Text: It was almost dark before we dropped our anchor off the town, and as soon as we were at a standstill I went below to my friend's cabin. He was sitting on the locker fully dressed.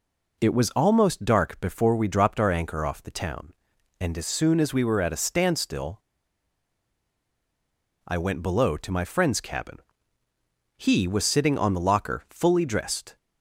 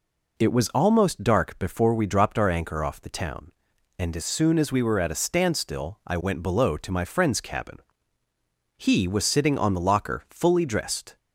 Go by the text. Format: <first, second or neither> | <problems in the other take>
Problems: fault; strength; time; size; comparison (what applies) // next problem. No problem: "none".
second | pauses between "standstill" and "I"; strong; at 6.0 s; 2.0 s long